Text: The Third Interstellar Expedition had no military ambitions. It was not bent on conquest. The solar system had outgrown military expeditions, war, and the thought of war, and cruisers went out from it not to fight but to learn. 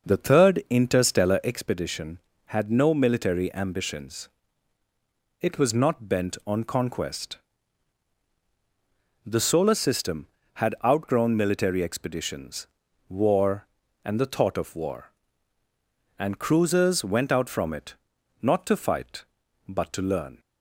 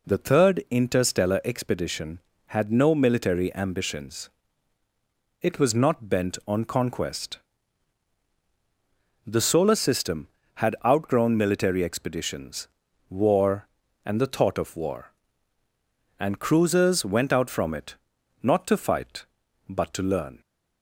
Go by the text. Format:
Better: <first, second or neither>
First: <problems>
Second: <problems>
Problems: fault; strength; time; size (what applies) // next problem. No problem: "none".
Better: second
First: starts louder than the rest; noticeable; until 1.7 s; 6 dB // pauses between "it" and "not"; noticeable; at 17.9 s; 0.46 s long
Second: pauses between "it" and "not"; noticeable; at 17.9 s; 0.46 s long